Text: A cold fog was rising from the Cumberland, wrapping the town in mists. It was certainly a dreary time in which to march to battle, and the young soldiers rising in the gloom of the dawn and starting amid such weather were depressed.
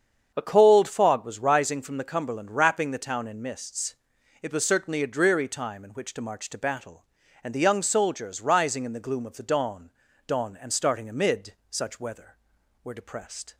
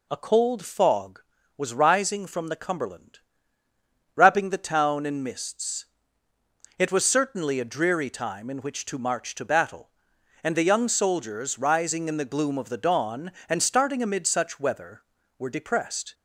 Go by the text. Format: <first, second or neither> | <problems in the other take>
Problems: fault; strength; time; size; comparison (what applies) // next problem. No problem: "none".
second | starts louder than the rest; strong; until 1.3 s; 7.5 dB // says "dawn" twice; at 10.2 s // pauses between "amid" and "such"; slight; at 11.5 s; 0.16 s long